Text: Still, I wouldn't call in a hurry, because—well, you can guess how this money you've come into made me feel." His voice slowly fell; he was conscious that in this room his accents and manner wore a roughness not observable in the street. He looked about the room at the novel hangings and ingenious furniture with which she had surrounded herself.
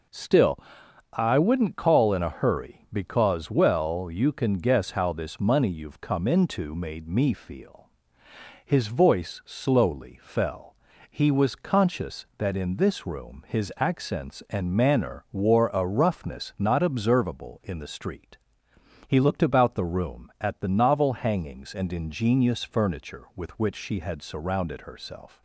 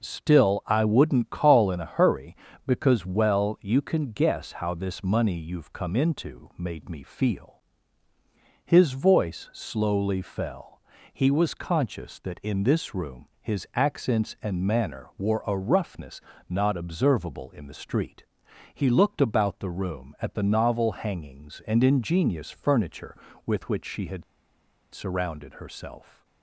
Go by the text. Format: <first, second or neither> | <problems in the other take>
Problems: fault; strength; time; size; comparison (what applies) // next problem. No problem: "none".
first | pauses between "roughness" and "not"; slight; at 16.1 s; 0.30 s long // pauses between "had" and "surrounded"; noticeable; at 24.2 s; 0.69 s long